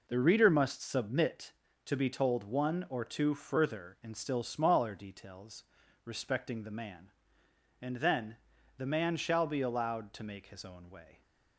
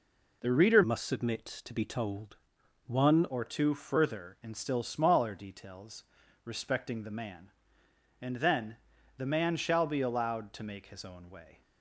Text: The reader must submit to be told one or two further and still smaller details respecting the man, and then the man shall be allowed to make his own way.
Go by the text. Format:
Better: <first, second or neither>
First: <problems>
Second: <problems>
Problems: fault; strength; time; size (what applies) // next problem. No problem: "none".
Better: first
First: pauses between "details" and "respecting"; at 5.6 s; 0.42 s long // pauses between "then" and "the"; at 8.3 s; 0.40 s long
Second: changes voice from "must" to "one"; from 0.8 to 3.2 s; 2.4 s long // pauses between "told" and "one"; noticeable; at 2.3 s; 0.50 s long // pauses between "details" and "respecting"; at 6.0 s; 0.42 s long // pauses between "then" and "the"; at 8.7 s; 0.40 s long